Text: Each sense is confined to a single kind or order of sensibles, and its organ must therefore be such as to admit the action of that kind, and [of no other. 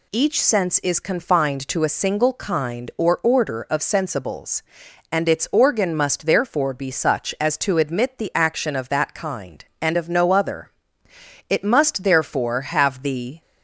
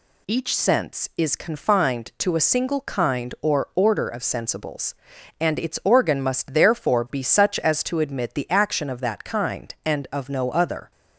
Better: second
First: goes on to say "It must therefore have the"; strong; from 11.4 s on; 1.9 s long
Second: none

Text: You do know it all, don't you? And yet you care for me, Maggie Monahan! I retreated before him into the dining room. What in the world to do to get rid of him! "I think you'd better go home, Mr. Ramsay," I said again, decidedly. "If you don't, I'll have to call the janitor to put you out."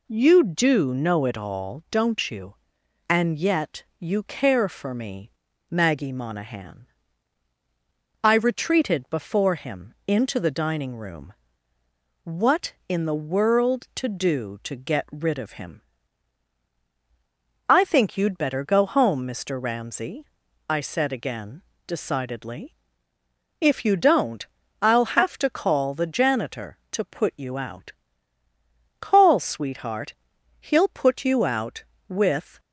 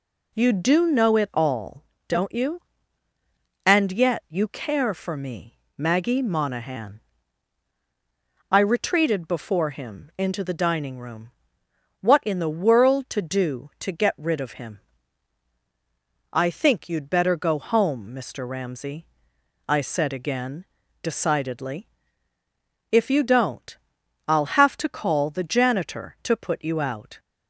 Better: second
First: pauses between "yet" and "you"; slight; at 3.8 s; 0.16 s long // goes on to say "Call sweetheart He'll put you out with"; strong; from 29.0 s on; 3.5 s long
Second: none

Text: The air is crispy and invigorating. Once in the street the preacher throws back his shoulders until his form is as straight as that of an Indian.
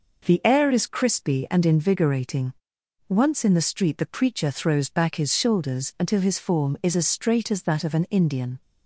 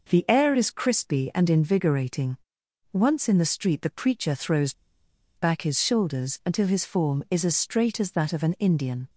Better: first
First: none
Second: pauses between "throws" and "back"; noticeable; at 4.7 s; 0.65 s long

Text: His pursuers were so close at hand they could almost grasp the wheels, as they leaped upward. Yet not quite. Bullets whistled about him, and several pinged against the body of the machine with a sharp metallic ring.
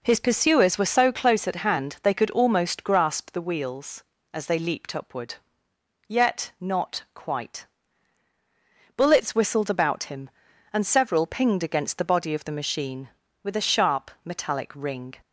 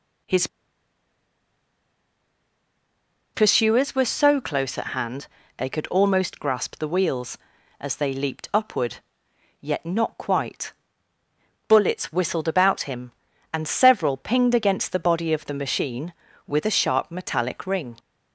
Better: first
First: none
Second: pauses between "His" and "pursuers"; strong; at 0.4 s; 2.8 s long // pauses between "hand" and "they"; slight; at 5.2 s; 0.30 s long

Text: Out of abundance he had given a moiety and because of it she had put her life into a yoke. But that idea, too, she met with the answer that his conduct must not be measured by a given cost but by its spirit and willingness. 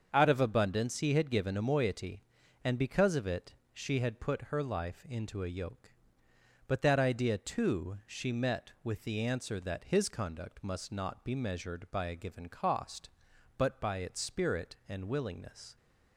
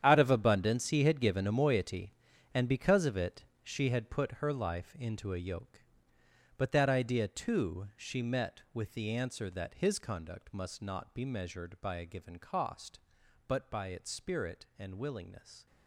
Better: first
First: starts louder than the rest; until 1.1 s; 7 dB // pauses between "it" and "she"; slight; at 3.5 s; 0.20 s long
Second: gets quieter; strong; throughout; 13.5 dB // starts louder than the rest; strong; until 1.0 s; 9.5 dB // pauses between "it" and "she"; slight; at 3.4 s; 0.20 s long

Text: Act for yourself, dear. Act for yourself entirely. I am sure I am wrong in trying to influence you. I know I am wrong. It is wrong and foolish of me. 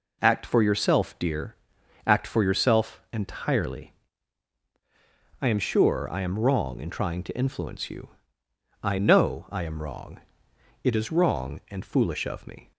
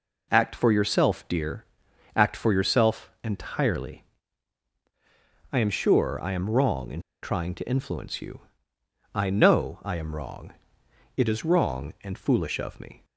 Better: first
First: none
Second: pauses between "in" and "trying"; slight; at 7.0 s; 0.22 s long

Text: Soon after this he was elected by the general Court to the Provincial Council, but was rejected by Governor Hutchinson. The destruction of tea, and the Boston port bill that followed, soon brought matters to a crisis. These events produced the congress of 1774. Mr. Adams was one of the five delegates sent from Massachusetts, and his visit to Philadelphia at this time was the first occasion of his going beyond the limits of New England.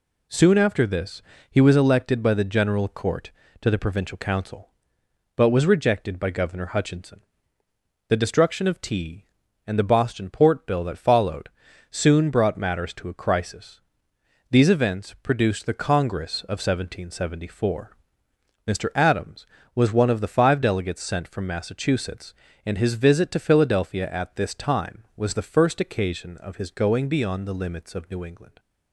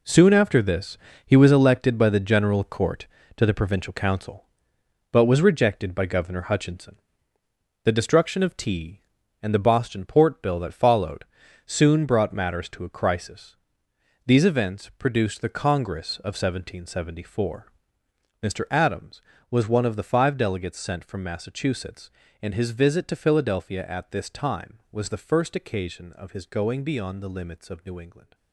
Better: first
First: pauses between "this" and "he"; slight; at 1.2 s; 0.28 s long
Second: gets quieter; strong; throughout; 10.5 dB // pauses between "this" and "he"; slight; at 0.9 s; 0.28 s long

